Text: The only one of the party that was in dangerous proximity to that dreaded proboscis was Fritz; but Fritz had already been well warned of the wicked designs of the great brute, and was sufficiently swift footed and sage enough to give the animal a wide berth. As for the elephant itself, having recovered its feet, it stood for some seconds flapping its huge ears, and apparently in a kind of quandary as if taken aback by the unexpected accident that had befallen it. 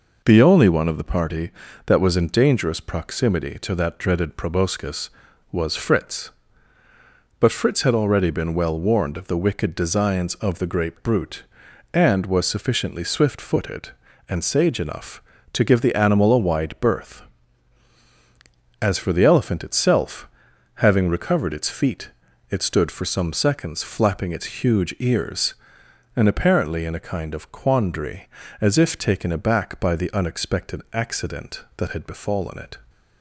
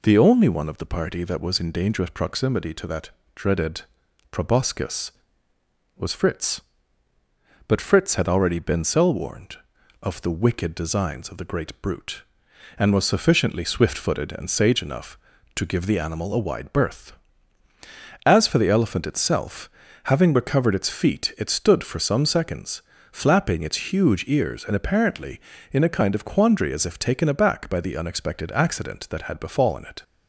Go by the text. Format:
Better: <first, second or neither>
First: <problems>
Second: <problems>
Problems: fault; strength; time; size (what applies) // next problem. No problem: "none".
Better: first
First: none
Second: pauses between "that" and "dreaded"; slight; at 3.1 s; 0.24 s long // pauses between "dreaded" and "proboscis"; noticeable; at 3.8 s; 0.48 s long // says "cell" for "well"; at 8.8 s // pauses between "seconds" and "flapping"; slight; at 22.8 s; 0.32 s long